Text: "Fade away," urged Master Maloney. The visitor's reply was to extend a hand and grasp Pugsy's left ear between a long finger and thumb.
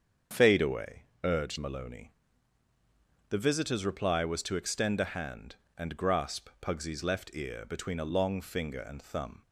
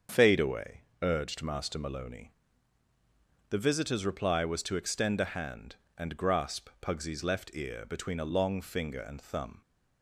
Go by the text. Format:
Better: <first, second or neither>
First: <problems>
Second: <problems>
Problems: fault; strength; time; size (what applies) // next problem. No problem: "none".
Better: second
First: starts louder than the rest; until 1.5 s; 7 dB // skips "Master"; at 1.5 s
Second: starts louder than the rest; until 1.3 s; 7 dB